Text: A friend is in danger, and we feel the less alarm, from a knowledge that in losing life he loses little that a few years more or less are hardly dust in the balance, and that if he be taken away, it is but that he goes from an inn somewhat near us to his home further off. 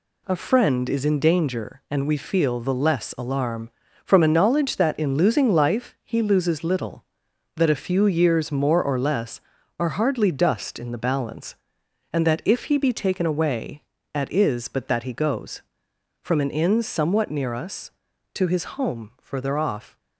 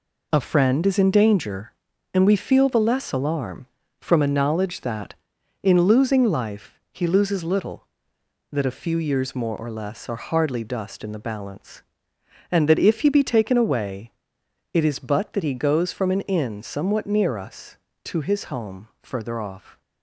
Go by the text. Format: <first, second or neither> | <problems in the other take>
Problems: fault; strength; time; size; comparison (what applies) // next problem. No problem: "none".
second | says "at" for "it"; at 14.1 s // pauses between "his" and "home"; slight; at 18.6 s; 0.16 s long